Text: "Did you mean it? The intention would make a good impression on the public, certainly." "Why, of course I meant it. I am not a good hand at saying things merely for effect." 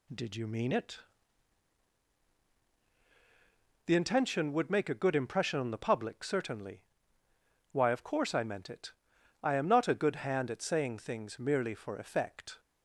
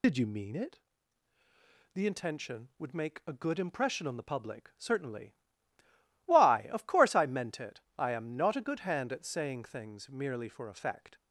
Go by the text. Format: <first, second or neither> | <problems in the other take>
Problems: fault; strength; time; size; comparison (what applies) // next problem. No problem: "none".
first | loses the start of "Did"; at 0.0 s; 65 ms